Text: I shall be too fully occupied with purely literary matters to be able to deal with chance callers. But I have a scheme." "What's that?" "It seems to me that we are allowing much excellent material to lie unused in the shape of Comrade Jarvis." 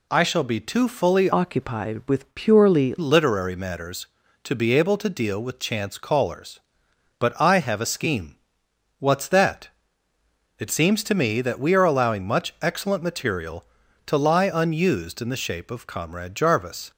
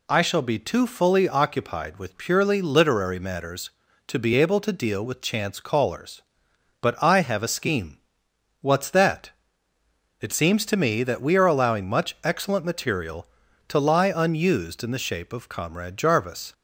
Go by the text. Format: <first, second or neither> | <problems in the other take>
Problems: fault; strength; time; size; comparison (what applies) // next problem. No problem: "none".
second | changes voice from "occupied" to "purely"; from 1.3 to 2.9 s; 1.6 s long